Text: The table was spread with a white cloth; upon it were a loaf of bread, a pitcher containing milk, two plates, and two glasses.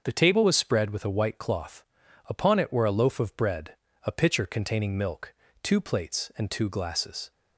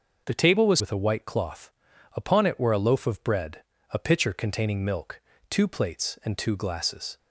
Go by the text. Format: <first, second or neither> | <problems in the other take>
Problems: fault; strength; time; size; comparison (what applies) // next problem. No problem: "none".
first | starts louder than the rest; noticeable; until 1.2 s; 6 dB; also in the first // skips "spread"; at 0.8 s